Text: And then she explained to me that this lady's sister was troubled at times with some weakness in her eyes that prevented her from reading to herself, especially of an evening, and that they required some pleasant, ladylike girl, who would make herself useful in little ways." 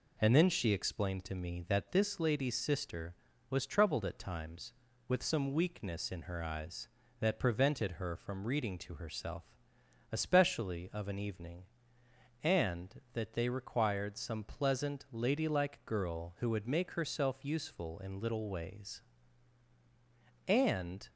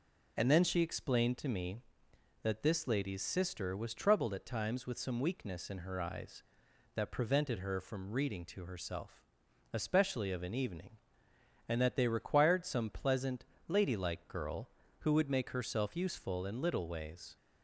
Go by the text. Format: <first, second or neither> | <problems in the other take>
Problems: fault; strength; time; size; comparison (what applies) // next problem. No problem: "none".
second | goes on to say "And"; noticeable; from 20.4 s on; 0.62 s long